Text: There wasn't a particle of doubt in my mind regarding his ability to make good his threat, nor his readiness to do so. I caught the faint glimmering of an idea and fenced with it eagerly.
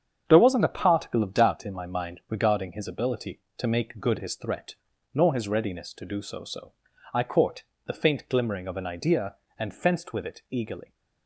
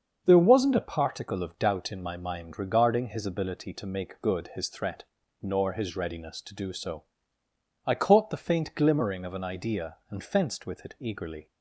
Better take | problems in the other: second | starts louder than the rest; strong; until 1.2 s; 8 dB; also in the second // says "so" twice; at 6.4 s // pauses between "caught" and "the"; slight; at 7.6 s; 0.24 s long

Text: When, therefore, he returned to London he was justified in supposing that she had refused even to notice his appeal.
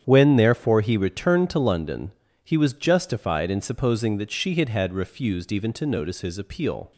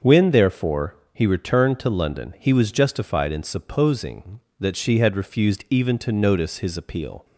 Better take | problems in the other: second | starts louder than the rest; strong; until 1.0 s; 9 dB; also in the second // pauses between "London" and "he"; slight; at 2.1 s; 0.36 s long // says "had" twice; at 4.6 s

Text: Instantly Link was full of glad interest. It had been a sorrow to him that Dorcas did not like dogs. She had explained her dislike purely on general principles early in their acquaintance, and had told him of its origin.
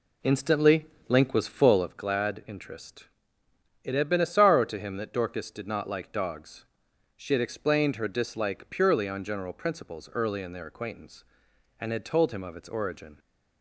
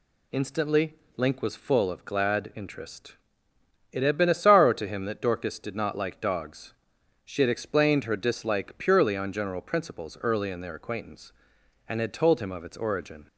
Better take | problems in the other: second | starts louder than the rest; slight; until 2.0 s; 3 dB // pauses between "Instantly" and "Link"; slight; at 0.8 s; 0.20 s long; slight in the second

